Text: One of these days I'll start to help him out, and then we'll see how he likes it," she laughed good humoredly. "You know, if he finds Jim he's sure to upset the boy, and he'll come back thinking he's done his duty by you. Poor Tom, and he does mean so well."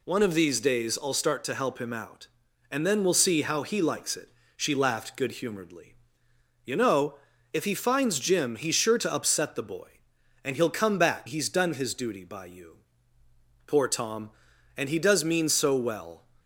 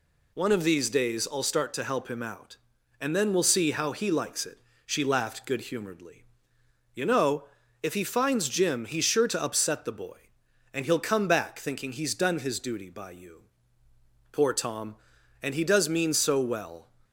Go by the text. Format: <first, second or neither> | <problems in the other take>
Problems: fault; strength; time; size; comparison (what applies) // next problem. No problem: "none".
second | skips "thinking"; at 11.2 s